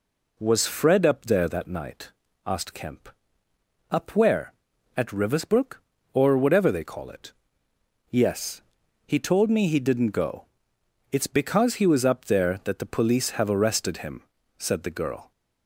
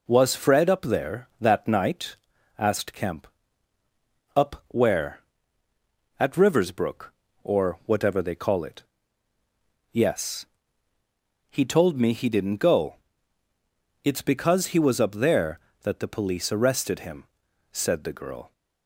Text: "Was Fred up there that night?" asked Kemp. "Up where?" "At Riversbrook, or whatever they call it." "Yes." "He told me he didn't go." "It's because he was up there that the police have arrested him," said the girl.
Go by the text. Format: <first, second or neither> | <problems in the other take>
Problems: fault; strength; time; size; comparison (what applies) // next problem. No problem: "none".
first | skips "have"; at 16.5 s